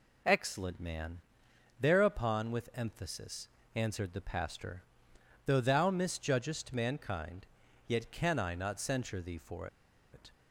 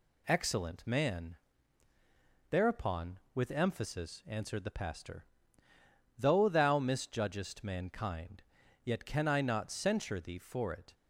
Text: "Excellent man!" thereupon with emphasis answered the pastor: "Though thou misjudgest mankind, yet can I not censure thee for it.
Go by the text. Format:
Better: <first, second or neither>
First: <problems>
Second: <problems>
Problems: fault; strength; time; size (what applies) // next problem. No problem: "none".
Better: second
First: pauses between "emphasis" and "answered"; slight; at 3.4 s; 0.26 s long // pauses between "for" and "it"; noticeable; at 9.6 s; 0.46 s long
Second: none